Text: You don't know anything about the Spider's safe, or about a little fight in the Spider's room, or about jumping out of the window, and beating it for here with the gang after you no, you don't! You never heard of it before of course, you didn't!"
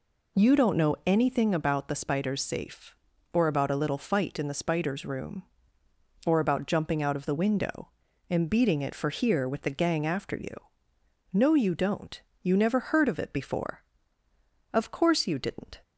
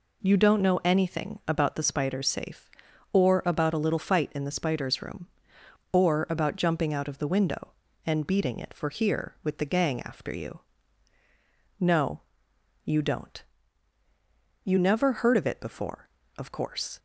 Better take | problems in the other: first | pauses between "you" and "no"; at 10.5 s; 1.2 s long; noticeable in the first // stops before "you didn't"; at 16.9 s

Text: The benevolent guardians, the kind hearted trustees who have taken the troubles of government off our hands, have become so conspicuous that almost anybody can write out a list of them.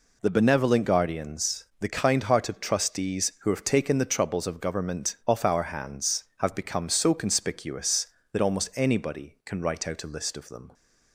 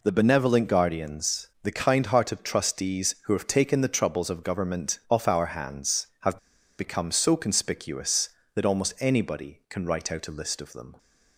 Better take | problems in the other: first | pauses between "have" and "become"; at 6.3 s; 0.40 s long

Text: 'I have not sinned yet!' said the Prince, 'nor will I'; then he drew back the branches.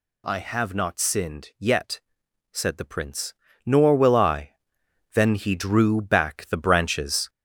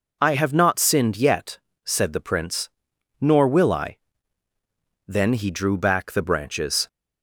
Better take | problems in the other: second | gets louder; noticeable; throughout; 4.5 dB

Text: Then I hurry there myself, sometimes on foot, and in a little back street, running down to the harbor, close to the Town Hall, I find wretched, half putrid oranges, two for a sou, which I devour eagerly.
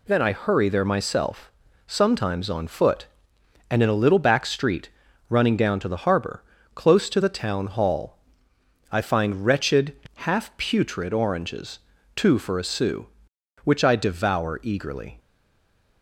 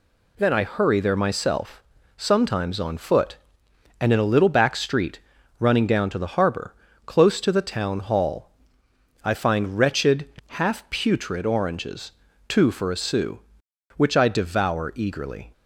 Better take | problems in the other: second | stays silent after the last word; slight; from 15.1 s on; 0.9 s long

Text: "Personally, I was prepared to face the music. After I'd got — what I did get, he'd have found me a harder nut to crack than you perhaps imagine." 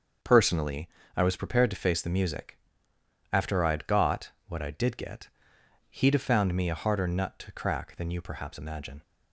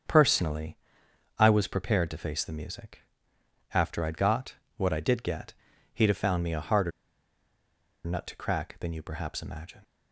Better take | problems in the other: first | starts louder than the rest; strong; until 1.6 s; 7.5 dB; also in the first // pauses between "harder" and "nut"; at 6.9 s; 1.1 s long

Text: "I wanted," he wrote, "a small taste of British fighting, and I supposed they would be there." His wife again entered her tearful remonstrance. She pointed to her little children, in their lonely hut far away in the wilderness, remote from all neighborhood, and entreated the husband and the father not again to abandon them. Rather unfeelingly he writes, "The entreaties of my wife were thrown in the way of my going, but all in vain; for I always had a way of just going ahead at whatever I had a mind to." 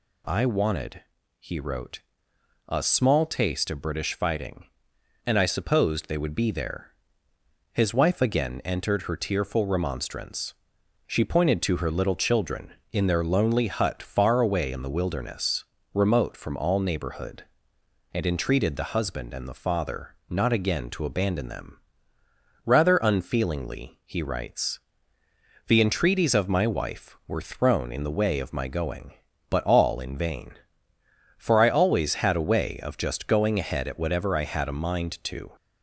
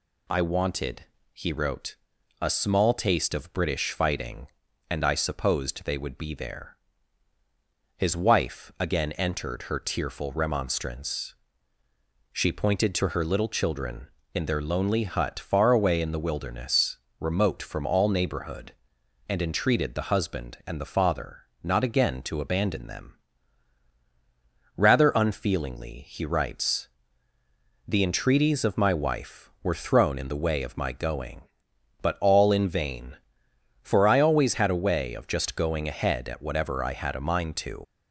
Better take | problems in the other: first | pauses between "father" and "not"; slight; at 21.4 s; 0.20 s long // leaves "to" unfinished; at 37.8 s; 105 ms

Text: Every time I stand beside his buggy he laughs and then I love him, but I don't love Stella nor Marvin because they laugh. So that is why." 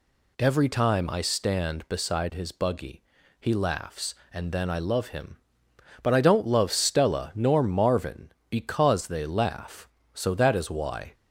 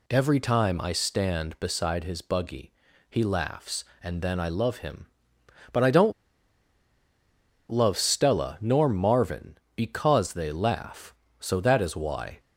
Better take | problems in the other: first | pauses between "buggy" and "he"; at 2.7 s; 0.38 s long; also in the first // pauses between "don't" and "love"; strong; at 6.1 s; 1.5 s long

